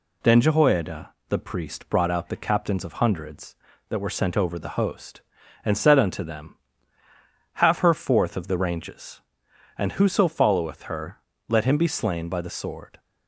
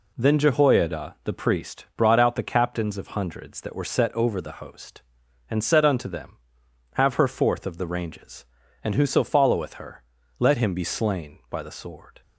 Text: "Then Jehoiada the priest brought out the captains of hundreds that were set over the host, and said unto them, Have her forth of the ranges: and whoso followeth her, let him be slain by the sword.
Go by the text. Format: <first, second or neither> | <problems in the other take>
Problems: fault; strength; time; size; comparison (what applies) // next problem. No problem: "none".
second | pauses between "Jehoiada" and "the"; slight; at 1.1 s; 0.16 s long // says "sent" for "set"; at 4.1 s